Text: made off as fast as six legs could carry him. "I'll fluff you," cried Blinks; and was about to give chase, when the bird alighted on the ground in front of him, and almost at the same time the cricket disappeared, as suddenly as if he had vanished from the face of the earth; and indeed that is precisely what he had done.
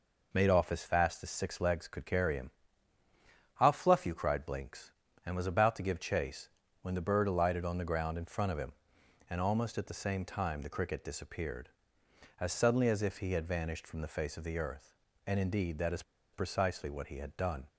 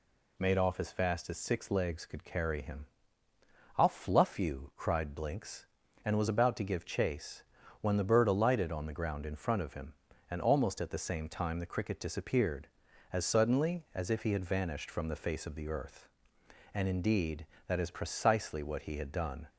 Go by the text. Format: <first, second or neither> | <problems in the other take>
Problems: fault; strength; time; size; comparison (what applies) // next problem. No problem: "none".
second | pauses between "is" and "precisely"; slight; at 16.0 s; 0.31 s long